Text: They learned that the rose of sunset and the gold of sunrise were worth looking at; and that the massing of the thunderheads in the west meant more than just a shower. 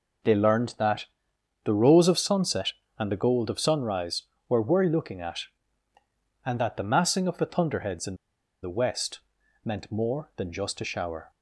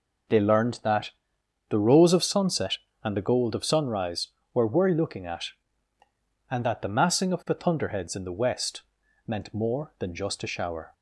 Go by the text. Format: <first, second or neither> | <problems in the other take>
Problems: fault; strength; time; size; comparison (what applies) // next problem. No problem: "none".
second | pauses between "that" and "the"; noticeable; at 1.0 s; 0.58 s long; noticeable in the second // pauses between "in" and "the"; noticeable; at 8.1 s; 0.46 s long // pauses between "west" and "meant"; at 9.2 s; 0.44 s long; also in the second